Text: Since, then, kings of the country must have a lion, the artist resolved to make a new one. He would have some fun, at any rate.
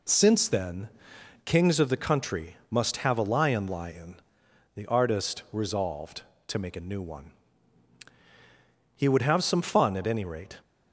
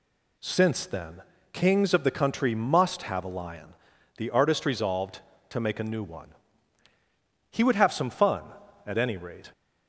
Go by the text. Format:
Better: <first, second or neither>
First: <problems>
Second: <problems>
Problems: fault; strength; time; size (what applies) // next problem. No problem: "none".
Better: second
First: says "lion" twice; at 3.6 s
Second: none